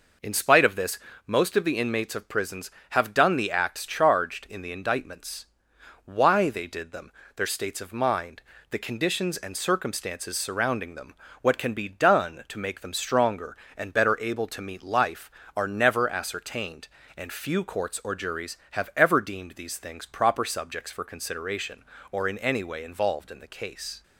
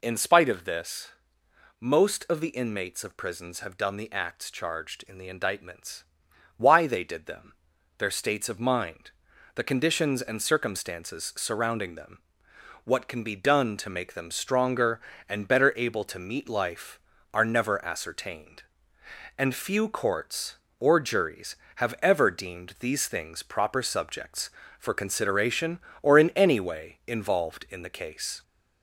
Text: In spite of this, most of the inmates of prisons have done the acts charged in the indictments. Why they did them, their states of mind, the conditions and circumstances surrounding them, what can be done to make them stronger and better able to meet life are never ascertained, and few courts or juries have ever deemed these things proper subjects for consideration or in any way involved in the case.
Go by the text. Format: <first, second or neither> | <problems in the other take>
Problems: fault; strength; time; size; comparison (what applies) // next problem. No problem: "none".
first | gets louder; slight; throughout; 3 dB